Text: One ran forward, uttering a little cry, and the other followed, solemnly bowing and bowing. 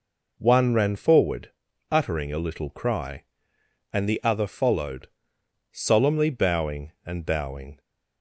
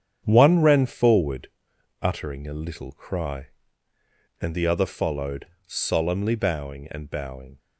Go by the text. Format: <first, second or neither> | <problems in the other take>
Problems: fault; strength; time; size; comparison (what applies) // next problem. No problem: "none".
first | gets quieter; strong; throughout; 8 dB